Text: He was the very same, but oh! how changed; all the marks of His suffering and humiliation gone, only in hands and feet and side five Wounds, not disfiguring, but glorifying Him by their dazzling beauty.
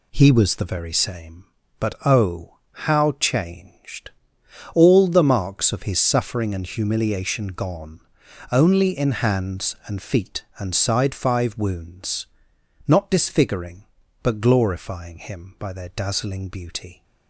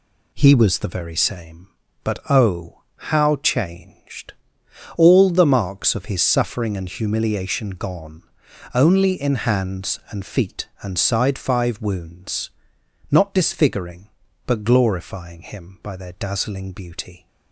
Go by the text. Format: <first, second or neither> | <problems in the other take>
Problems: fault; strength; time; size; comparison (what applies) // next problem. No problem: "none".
neither | none